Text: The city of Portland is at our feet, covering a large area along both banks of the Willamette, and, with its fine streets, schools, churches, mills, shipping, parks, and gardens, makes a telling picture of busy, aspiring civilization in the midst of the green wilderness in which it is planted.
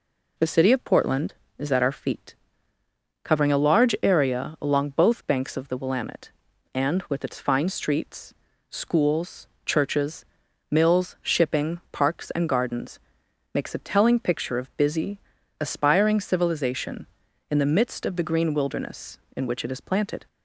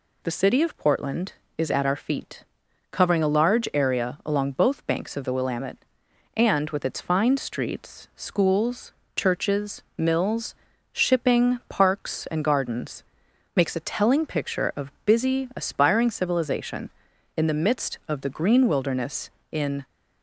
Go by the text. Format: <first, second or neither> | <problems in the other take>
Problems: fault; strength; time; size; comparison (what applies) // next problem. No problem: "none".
first | stops before "which it is planted"; at 19.8 s